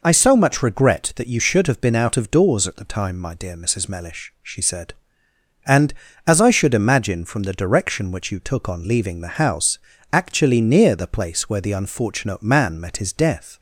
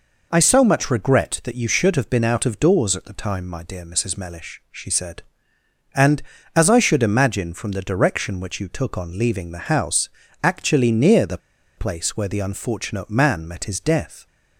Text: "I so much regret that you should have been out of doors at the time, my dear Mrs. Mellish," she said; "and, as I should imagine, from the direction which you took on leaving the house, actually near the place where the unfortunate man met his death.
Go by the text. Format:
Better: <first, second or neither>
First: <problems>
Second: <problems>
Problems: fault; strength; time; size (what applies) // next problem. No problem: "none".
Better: first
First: none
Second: pauses between "the" and "place"; at 11.3 s; 0.39 s long